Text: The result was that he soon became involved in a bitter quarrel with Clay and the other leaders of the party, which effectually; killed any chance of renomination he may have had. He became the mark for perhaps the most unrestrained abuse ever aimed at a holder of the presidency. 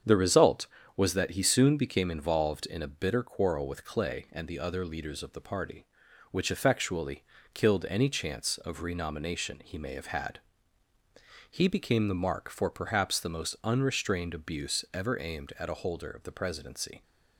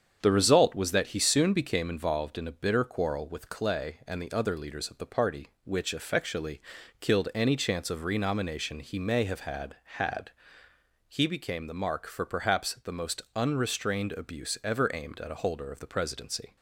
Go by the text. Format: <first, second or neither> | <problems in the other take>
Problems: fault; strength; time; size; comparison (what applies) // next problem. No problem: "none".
first | starts louder than the rest; strong; until 1.2 s; 7.5 dB; strong in the first // says "had" twice; at 9.8 s